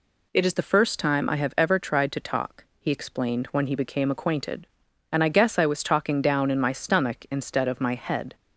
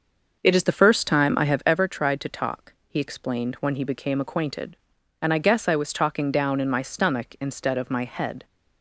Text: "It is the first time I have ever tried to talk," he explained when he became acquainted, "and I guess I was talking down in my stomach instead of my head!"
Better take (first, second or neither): first